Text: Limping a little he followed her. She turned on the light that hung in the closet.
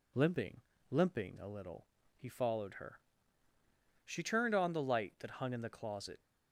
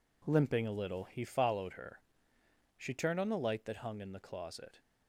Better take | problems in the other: second | says "Limping" twice; at 0.8 s // pauses between "little" and "he"; slight; at 1.8 s; 0.30 s long

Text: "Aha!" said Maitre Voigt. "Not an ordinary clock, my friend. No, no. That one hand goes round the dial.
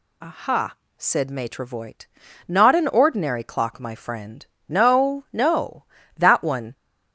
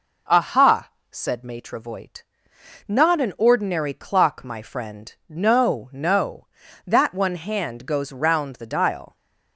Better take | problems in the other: second | stops before "hand goes round the dial"; at 6.7 s

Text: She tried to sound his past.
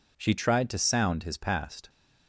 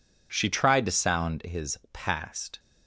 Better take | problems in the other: neither | none

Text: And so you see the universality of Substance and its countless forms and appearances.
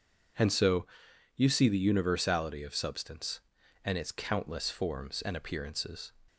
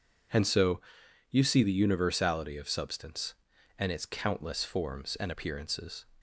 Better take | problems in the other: neither | pauses between "so" and "you"; noticeable; the same in both

